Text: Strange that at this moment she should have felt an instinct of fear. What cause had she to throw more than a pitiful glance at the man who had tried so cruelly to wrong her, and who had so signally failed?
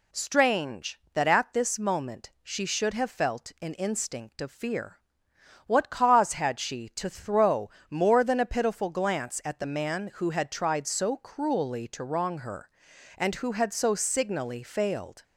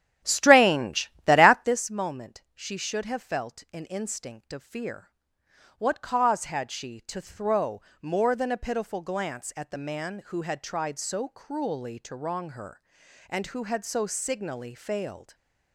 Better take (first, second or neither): first